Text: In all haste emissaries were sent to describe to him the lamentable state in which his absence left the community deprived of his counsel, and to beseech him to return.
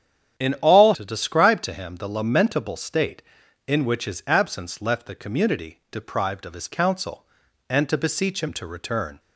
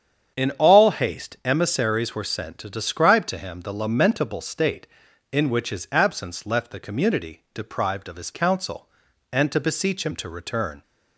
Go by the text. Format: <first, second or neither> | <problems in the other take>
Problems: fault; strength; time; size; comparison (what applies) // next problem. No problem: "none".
second | starts louder than the rest; strong; until 1.4 s; 9.5 dB; strong in the second // skips "haste emissaries were sent"; at 0.9 s